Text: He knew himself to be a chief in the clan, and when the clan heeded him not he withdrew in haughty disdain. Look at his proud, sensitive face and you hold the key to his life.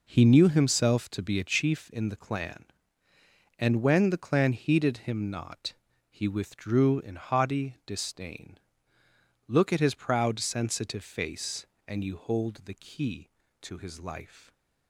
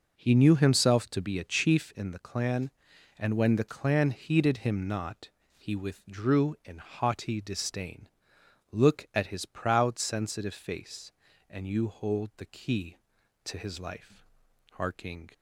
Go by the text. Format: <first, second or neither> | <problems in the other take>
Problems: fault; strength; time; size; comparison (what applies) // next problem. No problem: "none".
first | pauses between "not" and "he"; slight; at 5.2 s; 0.26 s long; slight in the first // goes on to say "Harking"; from 14.7 s on; 0.58 s long